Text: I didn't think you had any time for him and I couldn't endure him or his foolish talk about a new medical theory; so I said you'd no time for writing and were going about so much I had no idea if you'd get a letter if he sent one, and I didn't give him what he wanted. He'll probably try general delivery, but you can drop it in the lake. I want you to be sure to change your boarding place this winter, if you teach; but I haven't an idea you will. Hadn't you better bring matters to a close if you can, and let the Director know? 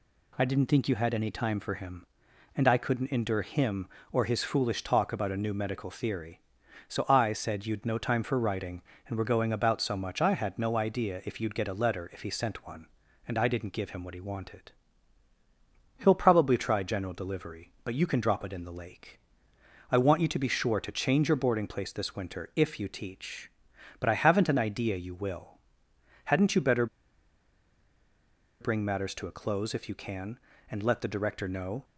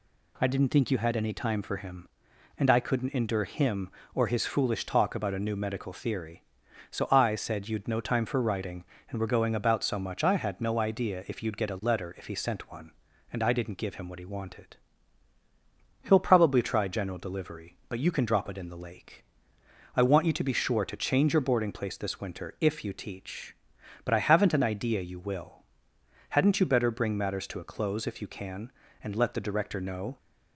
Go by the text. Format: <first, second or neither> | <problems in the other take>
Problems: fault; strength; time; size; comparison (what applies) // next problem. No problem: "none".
second | pauses between "better" and "bring"; strong; at 26.8 s; 1.7 s long